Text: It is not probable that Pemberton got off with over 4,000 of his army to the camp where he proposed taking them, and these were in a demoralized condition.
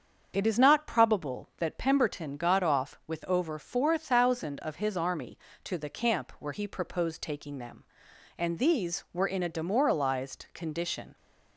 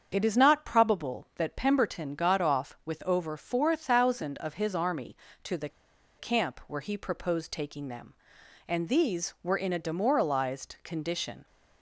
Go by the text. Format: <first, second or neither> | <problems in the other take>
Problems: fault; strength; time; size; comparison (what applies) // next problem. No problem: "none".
first | starts louder than the rest; until 1.1 s; 7 dB; also in the first // pauses between "the" and "camp"; noticeable; at 5.6 s; 0.49 s long